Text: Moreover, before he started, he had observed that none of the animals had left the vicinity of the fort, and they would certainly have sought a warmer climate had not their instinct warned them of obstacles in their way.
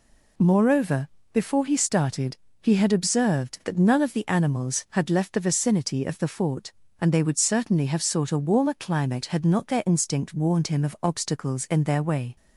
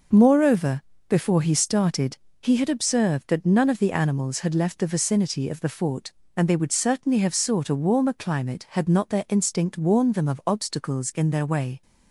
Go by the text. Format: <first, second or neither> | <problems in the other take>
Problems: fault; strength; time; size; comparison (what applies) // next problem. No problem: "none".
second | says "him" for "them"; at 10.6 s